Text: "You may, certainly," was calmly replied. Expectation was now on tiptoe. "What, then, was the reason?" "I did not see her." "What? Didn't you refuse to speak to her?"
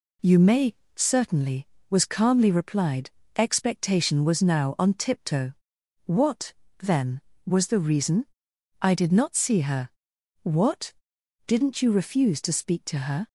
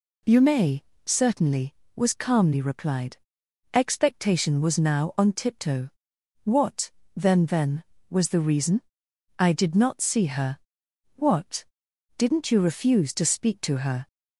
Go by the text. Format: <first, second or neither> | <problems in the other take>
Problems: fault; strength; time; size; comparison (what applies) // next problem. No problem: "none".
first | says "then" twice; at 7.4 s